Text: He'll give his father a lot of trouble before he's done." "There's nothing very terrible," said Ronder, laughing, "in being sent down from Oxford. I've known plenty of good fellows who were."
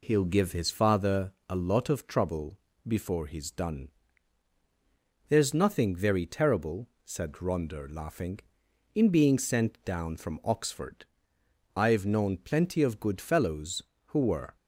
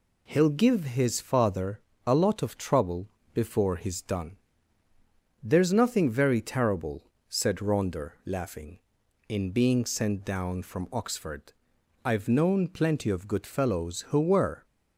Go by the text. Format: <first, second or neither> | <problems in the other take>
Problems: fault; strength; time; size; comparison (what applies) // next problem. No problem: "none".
neither | pauses between "father" and "a"; slight; the same in both // pauses between "trouble" and "before"; slight; the same in both